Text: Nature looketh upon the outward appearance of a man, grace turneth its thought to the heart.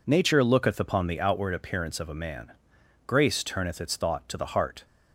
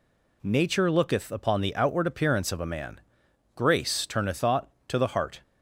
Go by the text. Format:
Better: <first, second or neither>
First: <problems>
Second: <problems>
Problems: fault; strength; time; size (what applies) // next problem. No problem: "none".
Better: first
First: none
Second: skips "its"; at 4.3 s